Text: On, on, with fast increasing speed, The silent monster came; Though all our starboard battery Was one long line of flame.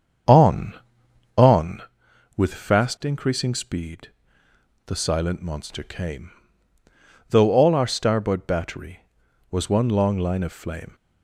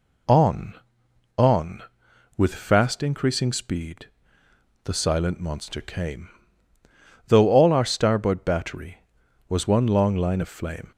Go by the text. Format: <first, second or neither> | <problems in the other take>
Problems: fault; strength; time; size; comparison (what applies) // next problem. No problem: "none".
second | starts louder than the rest; strong; until 1.9 s; 7.5 dB